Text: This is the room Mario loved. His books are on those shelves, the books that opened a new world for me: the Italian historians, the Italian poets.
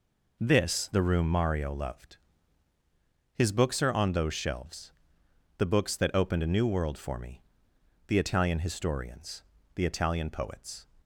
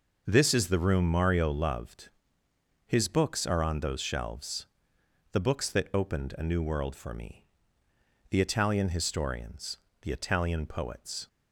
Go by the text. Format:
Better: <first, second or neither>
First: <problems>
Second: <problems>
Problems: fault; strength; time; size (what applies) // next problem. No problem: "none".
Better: second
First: skips "is"; at 0.8 s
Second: none